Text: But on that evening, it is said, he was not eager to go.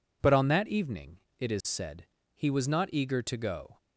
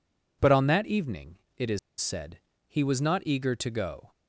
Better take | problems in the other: first | pauses between "is" and "said"; slight; at 1.7 s; 0.21 s long

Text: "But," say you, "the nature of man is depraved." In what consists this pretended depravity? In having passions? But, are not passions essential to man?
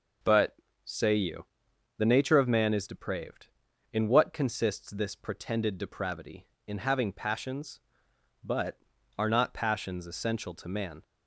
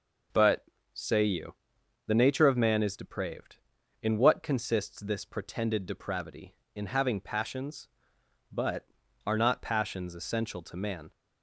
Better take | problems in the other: neither | none

